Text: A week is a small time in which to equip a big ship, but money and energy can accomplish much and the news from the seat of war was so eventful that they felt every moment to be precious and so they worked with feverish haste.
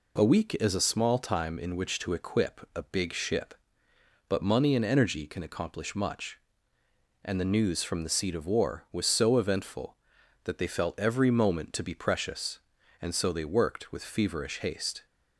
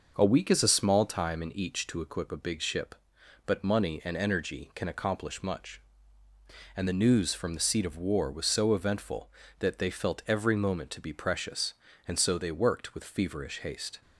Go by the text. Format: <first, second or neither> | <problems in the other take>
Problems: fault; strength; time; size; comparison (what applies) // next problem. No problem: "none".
first | says "each" for "which"; at 1.5 s